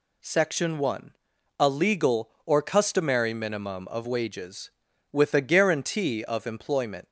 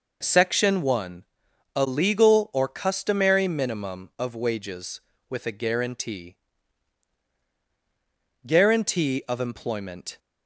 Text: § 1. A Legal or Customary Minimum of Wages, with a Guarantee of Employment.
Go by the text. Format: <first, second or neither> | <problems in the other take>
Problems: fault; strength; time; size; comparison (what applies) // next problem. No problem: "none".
first | says "Guarantee" twice; at 8.4 s